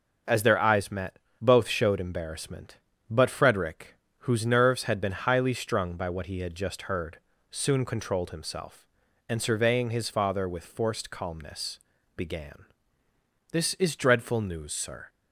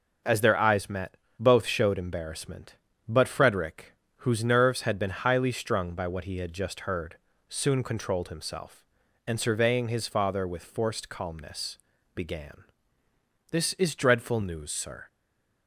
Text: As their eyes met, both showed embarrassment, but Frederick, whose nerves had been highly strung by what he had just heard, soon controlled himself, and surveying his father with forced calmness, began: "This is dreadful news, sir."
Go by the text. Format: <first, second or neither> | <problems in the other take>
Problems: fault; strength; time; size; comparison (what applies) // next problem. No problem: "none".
first | stays silent after the last word; slight; from 15.0 s on; 0.6 s long